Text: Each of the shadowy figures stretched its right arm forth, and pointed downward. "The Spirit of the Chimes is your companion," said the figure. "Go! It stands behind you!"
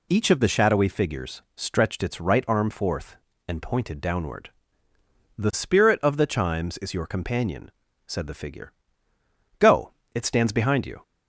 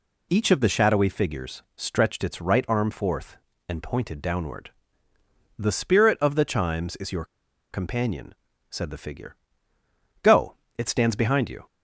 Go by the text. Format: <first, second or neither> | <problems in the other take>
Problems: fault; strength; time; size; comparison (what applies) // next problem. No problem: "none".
first | pauses between "your" and "companion"; noticeable; at 7.2 s; 0.46 s long